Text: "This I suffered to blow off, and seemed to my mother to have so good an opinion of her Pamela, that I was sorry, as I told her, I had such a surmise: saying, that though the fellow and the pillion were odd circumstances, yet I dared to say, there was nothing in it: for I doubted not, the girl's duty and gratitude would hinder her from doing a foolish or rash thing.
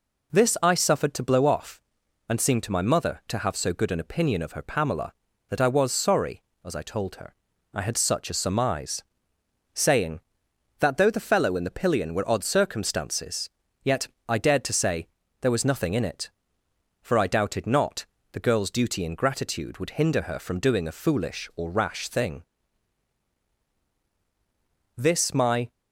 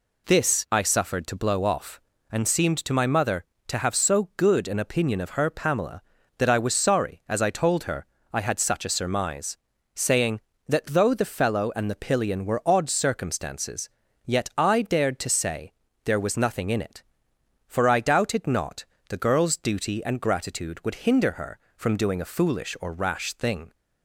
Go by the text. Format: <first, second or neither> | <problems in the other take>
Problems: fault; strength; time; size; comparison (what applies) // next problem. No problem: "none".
second | pauses between "yet" and "I"; slight; at 14.0 s; 0.22 s long // goes on to say "This my"; noticeable; from 24.9 s on; 0.76 s long